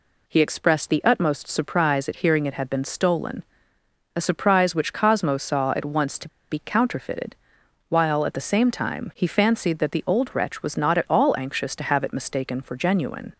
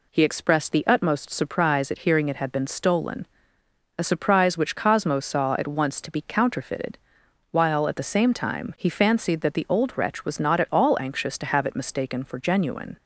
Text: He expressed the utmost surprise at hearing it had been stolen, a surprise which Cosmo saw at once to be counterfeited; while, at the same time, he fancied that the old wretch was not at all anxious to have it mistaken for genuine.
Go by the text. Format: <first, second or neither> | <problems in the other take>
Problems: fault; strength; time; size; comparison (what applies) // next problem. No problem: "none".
second | pauses between "to" and "be"; slight; at 6.2 s; 0.21 s long